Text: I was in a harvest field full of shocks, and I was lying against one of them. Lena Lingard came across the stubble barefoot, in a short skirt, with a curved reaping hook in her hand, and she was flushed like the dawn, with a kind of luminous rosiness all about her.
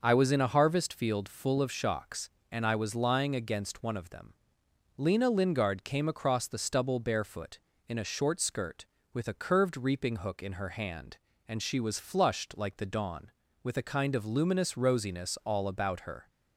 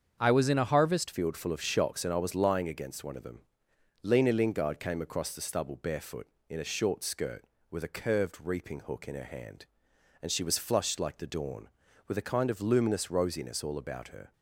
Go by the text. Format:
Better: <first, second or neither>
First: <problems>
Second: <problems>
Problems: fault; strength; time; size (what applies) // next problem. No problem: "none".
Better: first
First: starts louder than the rest; until 1.0 s; 6 dB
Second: starts louder than the rest; strong; until 1.2 s; 7 dB // changes voice at "field"; from 1.1 s on; 13.2 s long